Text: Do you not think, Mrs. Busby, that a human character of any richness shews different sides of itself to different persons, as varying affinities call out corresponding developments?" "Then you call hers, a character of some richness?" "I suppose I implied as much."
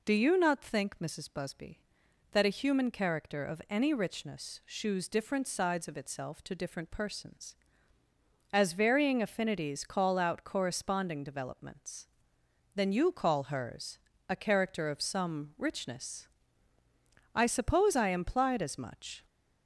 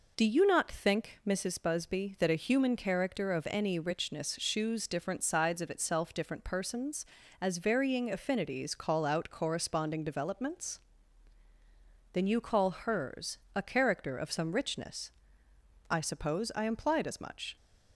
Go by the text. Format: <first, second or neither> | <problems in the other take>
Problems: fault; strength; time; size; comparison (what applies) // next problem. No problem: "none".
first | skips "to"; at 6.1 s